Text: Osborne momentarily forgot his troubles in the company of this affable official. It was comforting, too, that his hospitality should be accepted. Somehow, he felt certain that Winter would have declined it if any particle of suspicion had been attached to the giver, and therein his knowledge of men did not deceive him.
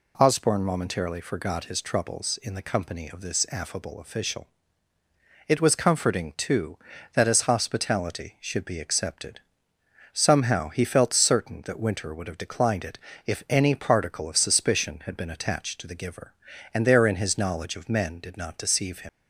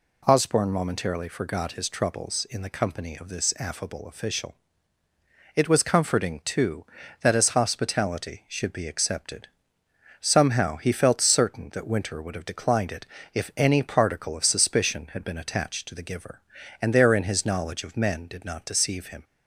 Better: second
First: pauses between "it" and "if"; slight; at 12.9 s; 0.28 s long // leaves "him" unfinished; at 19.0 s; 70 ms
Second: pauses between "it" and "if"; slight; at 13.0 s; 0.28 s long

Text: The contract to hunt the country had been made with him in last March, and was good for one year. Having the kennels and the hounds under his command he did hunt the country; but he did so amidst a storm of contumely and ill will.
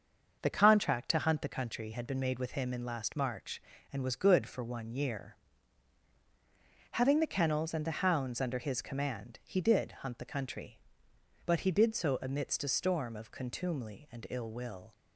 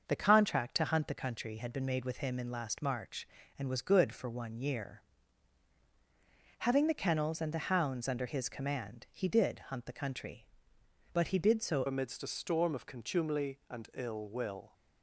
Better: first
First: starts louder than the rest; until 1.4 s; 6.5 dB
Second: starts louder than the rest; until 1.0 s; 6.5 dB // changes voice at "amidst"; from 11.8 s on; 2.9 s long

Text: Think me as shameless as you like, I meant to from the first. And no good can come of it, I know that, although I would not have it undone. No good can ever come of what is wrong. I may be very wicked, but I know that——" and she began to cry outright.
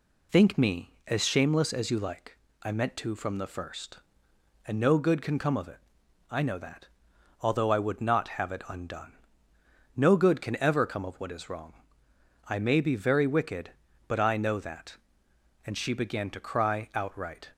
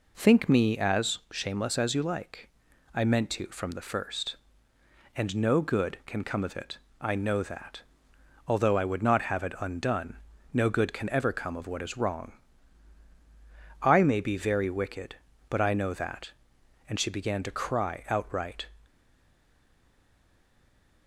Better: first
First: none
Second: stays silent after the last word; from 18.8 s on; 2.2 s long

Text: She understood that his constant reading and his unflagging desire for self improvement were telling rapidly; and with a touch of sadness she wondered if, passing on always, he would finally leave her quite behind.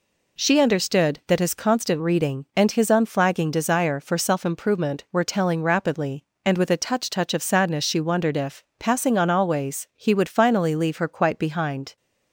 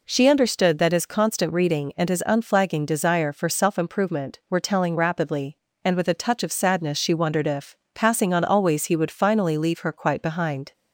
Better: second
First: says "touch" twice; at 7.0 s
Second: none

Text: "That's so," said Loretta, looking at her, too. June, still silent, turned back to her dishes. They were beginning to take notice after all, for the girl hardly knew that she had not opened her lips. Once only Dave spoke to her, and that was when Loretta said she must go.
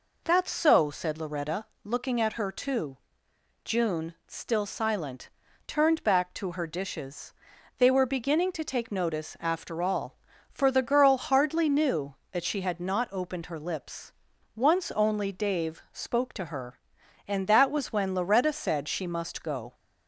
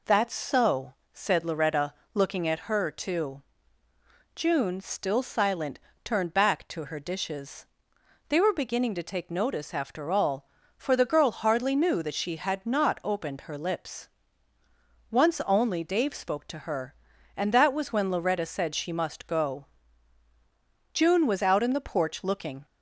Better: first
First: none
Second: goes on to say "June was out in the porch looking"; strong; from 20.9 s on; 1.7 s long

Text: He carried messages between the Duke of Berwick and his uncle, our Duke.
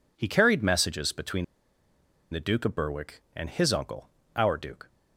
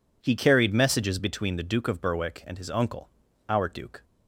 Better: second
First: pauses between "between" and "the"; noticeable; at 1.4 s; 0.86 s long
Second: none

